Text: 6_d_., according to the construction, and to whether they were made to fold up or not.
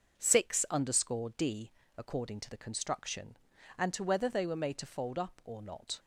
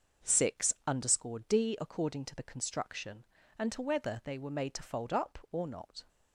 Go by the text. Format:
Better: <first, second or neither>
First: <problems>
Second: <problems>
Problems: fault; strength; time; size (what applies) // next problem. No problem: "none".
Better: neither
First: starts louder than the rest; until 1.2 s; 6.5 dB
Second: starts louder than the rest; until 1.3 s; 6.5 dB